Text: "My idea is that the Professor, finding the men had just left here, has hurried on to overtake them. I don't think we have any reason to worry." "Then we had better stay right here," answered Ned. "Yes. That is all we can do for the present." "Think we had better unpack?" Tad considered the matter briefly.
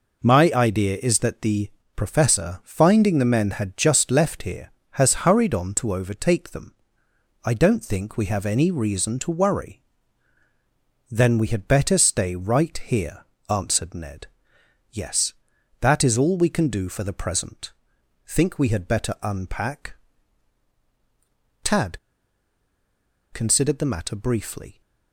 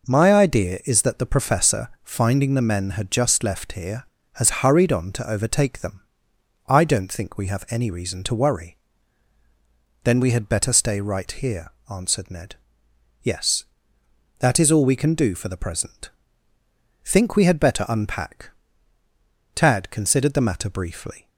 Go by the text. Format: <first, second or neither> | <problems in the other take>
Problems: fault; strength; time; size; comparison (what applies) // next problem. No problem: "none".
second | pauses between "the" and "Professor"; slight; at 1.7 s; 0.24 s long // pauses between "Tad" and "considered"; strong; at 21.9 s; 1.3 s long